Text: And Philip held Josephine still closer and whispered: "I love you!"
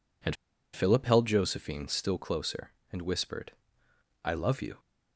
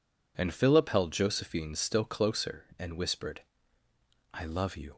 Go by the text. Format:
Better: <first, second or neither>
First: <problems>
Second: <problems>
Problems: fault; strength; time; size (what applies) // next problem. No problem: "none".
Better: second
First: pauses between "And" and "Philip"; at 0.3 s; 0.38 s long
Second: none